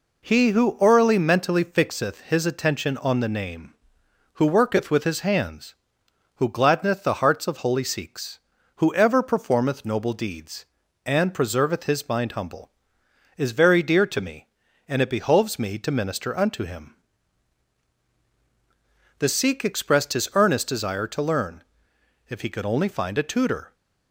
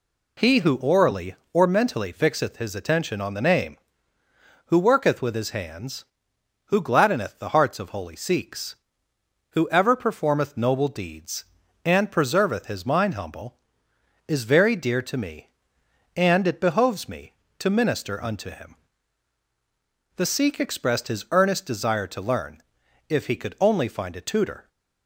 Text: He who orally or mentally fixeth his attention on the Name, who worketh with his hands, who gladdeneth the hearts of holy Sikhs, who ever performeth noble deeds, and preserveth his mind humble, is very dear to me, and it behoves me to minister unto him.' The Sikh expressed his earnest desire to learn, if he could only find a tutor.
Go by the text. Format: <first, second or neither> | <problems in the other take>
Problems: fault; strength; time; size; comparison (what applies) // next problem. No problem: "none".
second | skips "or"; at 1.1 s